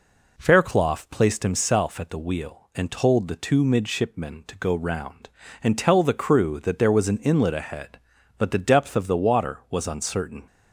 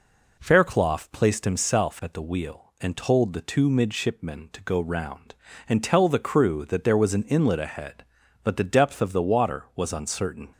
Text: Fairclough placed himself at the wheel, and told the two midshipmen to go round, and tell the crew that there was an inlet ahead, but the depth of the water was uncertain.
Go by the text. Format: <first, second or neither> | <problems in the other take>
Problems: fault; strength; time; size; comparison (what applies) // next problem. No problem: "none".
neither | none